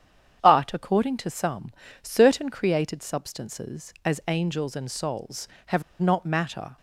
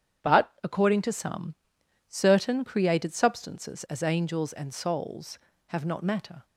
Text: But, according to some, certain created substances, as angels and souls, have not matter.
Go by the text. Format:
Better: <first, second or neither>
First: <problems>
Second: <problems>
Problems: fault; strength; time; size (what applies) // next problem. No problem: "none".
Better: second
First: starts louder than the rest; strong; until 1.4 s; 8.5 dB // pauses between "have" and "not"; slight; at 5.8 s; 0.17 s long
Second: starts louder than the rest; strong; until 1.3 s; 9 dB